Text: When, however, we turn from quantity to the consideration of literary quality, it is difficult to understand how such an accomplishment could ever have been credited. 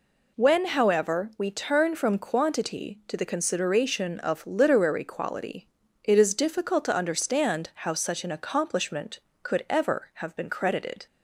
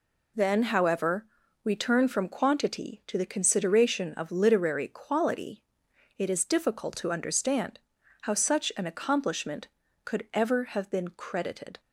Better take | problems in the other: first | says "Then" for "When"; at 0.3 s // pauses between "understand" and "how"; at 7.7 s; 0.42 s long

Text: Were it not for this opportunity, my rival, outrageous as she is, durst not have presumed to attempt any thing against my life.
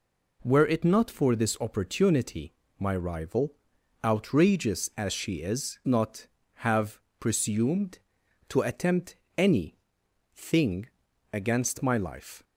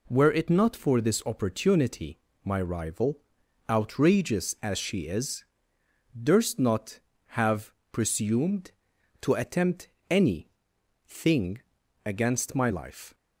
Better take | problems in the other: second | skips "durst"; at 5.8 s // pauses between "have" and "presumed"; slight; at 6.9 s; 0.18 s long; slight in the second // pauses between "attempt" and "any"; slight; at 9.1 s; 0.20 s long; slight in the second // pauses between "any" and "thing"; noticeable; at 9.7 s; 0.60 s long; noticeable in the second // pauses between "thing" and "against"; at 10.8 s; 0.44 s long; also in the second

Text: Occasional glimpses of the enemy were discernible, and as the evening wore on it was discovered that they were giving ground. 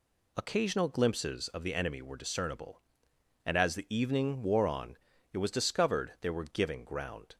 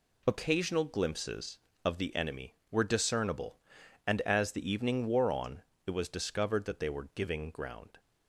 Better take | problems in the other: second | pauses between "on" and "it"; slight; at 4.9 s; 0.36 s long; slight in the second // skips "that"; at 6.1 s

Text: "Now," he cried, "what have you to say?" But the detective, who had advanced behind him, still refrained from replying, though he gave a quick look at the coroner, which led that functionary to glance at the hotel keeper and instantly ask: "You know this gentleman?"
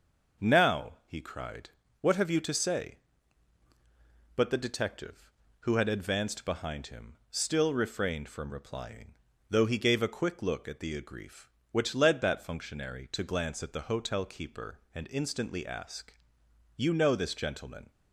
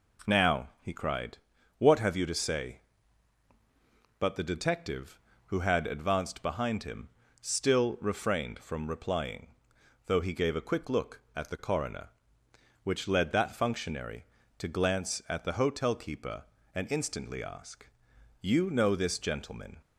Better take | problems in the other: second | says "agrief" for "coroner"; at 11.0 s

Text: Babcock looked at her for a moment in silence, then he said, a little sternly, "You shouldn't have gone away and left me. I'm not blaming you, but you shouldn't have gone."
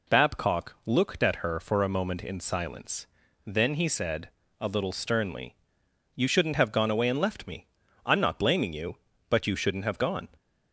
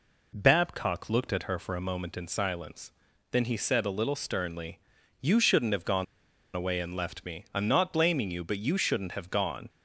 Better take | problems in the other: first | pauses between "gone" and "away"; noticeable; at 6.0 s; 0.51 s long

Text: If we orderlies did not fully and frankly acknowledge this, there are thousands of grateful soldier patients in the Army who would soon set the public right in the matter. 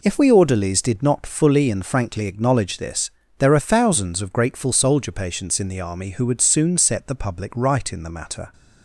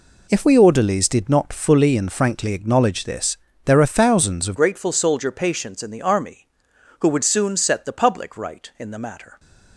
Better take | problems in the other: first | changes voice at "grateful"; from 4.5 s on; 4.8 s long

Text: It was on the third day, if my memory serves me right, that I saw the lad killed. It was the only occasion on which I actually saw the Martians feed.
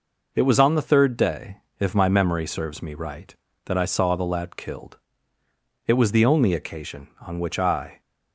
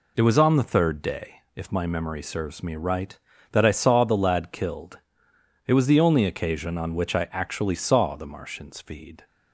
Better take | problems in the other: second | stops before "actually saw the Martians feed"; at 8.0 s

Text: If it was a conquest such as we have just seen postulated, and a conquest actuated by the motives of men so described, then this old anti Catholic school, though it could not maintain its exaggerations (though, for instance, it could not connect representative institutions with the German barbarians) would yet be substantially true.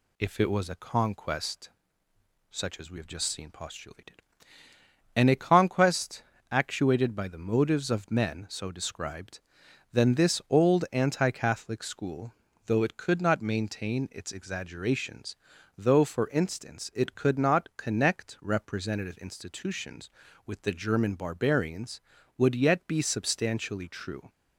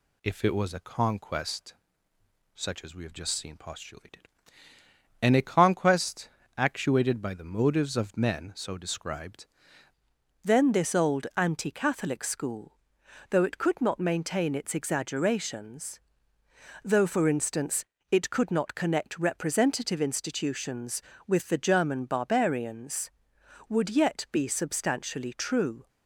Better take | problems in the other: first | pauses between "conquest" and "such"; noticeable; at 1.7 s; 0.80 s long; noticeable in the first // pauses between "conquest" and "actuated"; slight; at 6.2 s; 0.30 s long; slight in the first // changes voice at "then"; from 10.4 s on; 15.4 s long

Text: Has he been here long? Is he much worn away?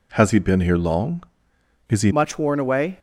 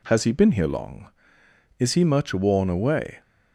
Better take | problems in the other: second | changes voice at "much"; from 2.1 s on; 0.8 s long

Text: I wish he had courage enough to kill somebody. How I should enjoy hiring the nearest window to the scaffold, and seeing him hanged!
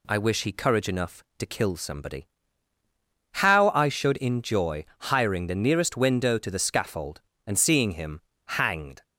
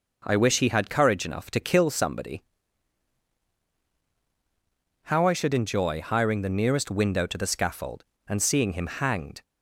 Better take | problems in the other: second | skips "had"; at 0.5 s // pauses between "enjoy" and "hiring"; slight; at 4.8 s; 0.16 s long // pauses between "him" and "hanged"; slight; at 8.2 s; 0.24 s long

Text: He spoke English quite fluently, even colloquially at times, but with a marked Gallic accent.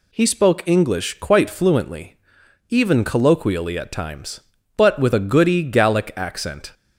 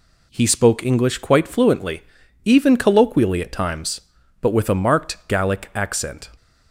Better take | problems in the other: second | says "goody" for "marked"; at 5.1 s

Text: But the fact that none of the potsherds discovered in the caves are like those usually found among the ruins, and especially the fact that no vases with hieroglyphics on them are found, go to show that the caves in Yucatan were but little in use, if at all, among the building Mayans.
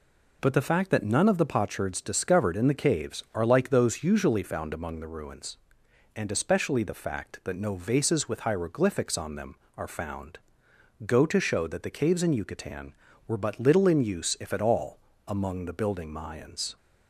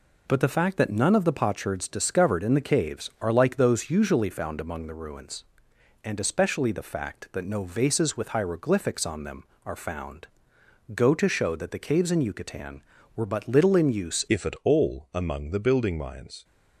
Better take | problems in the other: first | changes voice at "if"; from 14.2 s on; 2.2 s long

